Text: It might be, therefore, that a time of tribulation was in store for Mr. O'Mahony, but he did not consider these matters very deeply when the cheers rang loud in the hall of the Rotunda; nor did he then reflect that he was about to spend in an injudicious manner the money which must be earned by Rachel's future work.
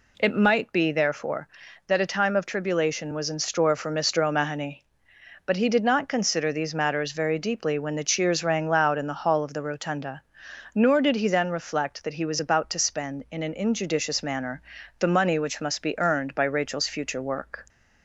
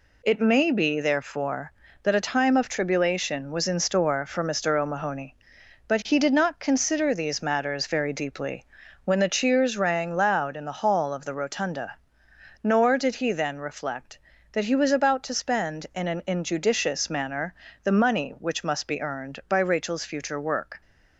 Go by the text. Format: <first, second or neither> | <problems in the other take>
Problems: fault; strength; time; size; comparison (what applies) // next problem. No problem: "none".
first | says "may" for "might"; at 0.4 s // pauses between "deeply" and "when"; at 8.6 s; 0.38 s long // pauses between "manner" and "the"; slight; at 17.5 s; 0.28 s long; also in the first